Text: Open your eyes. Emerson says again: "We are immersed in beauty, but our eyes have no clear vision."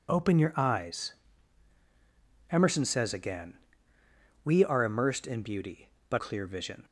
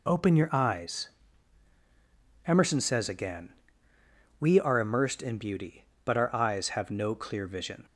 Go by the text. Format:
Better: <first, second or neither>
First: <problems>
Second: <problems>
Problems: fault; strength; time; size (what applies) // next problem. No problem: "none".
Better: second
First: skips "our eyes have no"; at 6.1 s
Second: none